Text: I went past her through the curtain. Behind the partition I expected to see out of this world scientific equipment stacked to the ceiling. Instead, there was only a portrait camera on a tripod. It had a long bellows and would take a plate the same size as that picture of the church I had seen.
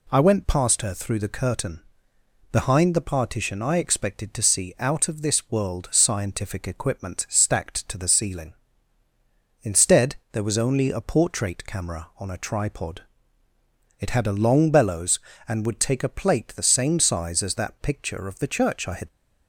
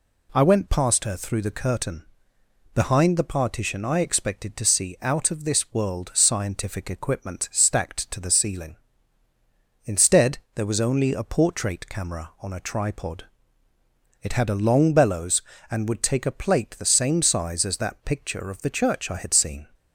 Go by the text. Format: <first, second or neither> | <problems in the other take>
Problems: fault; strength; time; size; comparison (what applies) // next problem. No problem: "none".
second | stops before "seen"; at 19.0 s